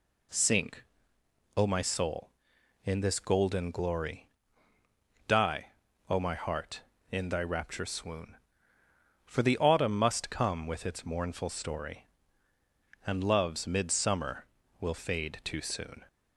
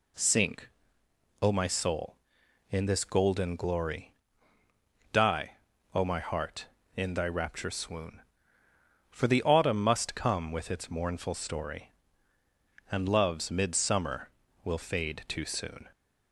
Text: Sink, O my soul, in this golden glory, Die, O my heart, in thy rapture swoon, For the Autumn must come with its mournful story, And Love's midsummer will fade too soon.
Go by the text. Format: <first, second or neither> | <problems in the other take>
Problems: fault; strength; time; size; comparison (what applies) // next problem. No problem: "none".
neither | none